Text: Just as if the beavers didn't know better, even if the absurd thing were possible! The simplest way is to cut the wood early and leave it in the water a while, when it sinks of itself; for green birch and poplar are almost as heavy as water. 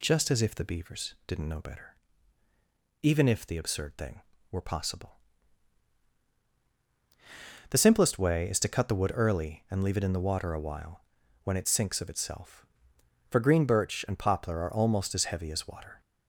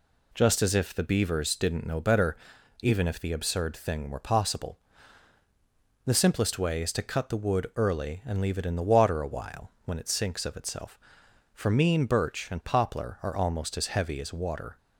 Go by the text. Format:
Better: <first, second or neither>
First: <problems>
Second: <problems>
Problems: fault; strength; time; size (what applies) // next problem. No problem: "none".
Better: first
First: none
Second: says "mean" for "green"; at 11.7 s